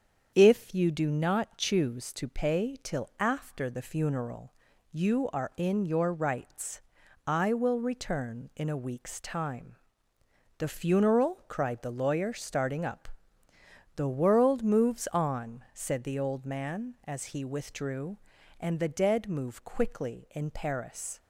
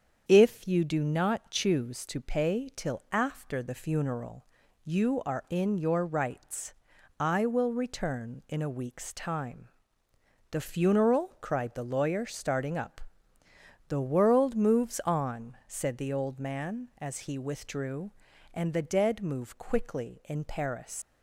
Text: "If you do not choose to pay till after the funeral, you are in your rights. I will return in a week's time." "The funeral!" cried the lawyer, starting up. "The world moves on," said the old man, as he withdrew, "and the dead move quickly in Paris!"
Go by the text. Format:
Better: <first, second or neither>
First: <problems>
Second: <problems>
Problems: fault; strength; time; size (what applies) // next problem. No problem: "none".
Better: first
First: starts louder than the rest; strong; until 1.3 s; 7.5 dB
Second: starts louder than the rest; strong; until 1.2 s; 7.5 dB // leaves "Paris" unfinished; at 21.0 s; 105 ms